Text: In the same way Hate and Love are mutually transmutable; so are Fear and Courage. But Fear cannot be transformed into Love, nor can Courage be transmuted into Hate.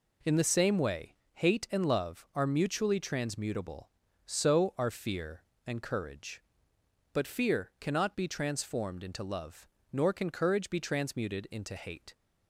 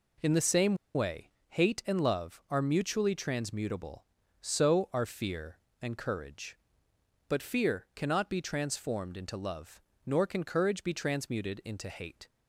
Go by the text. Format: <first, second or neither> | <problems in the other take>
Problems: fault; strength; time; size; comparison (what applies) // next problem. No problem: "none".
first | pauses between "same" and "way"; slight; at 0.7 s; 0.20 s long // pauses between "way" and "Hate"; slight; at 1.3 s; 0.18 s long; slight in the first